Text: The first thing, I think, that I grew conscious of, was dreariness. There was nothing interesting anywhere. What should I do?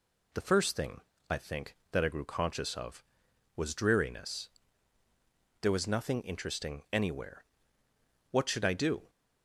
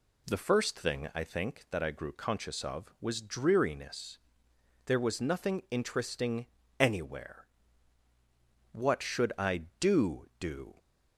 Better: first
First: none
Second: pauses between "interesting" and "anywhere"; slight; at 6.4 s; 0.32 s long // says "do" twice; at 10.3 s

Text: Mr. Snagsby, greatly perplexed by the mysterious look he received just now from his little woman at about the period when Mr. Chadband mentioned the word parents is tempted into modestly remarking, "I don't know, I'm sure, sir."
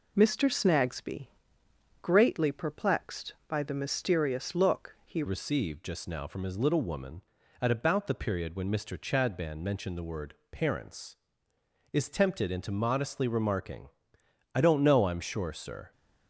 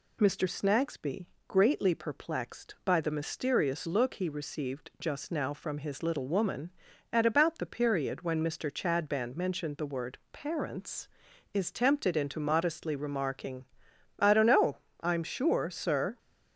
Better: second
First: changes voice at "received"; from 5.2 s on; 10.7 s long // pauses between "word" and "parents"; slight; at 10.3 s; 0.16 s long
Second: none

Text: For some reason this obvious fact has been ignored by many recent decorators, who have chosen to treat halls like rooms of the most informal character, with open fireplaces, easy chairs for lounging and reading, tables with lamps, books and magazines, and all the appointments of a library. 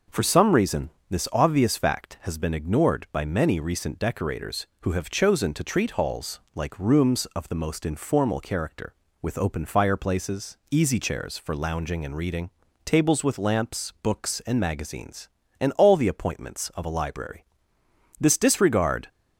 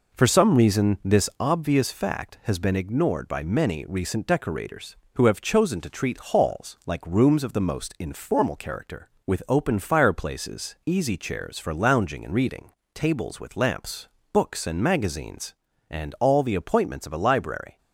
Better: second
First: pauses between "reason" and "this"; slight; at 0.8 s; 0.22 s long // goes on to say "This disregard"; noticeable; from 18.1 s on; 0.88 s long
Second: none

